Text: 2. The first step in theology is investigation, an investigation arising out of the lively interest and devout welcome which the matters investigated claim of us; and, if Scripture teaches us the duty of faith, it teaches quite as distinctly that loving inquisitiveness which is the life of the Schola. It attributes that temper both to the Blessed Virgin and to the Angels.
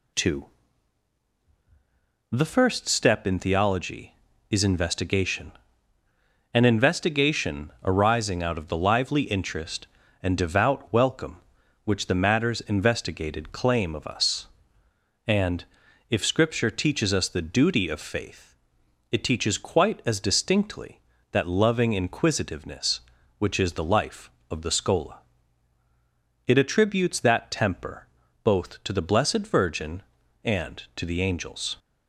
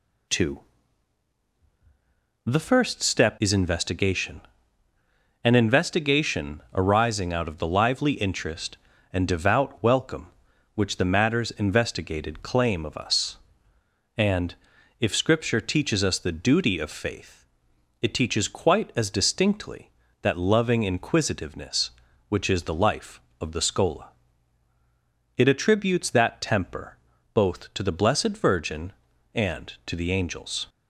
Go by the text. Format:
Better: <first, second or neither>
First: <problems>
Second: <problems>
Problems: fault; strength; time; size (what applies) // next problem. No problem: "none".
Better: first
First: pauses between "temper" and "both"; at 28.0 s; 0.38 s long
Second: skips "in theology"; at 3.3 s // pauses between "temper" and "both"; at 26.9 s; 0.38 s long